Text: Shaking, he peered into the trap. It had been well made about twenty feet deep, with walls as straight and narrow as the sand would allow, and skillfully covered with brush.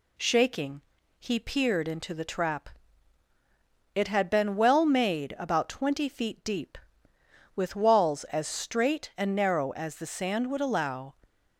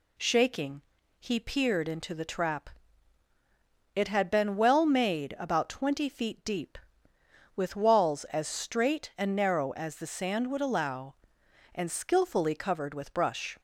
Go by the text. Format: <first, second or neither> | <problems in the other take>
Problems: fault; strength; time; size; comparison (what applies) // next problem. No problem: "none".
second | stops before "and skillfully covered with brush"; at 11.2 s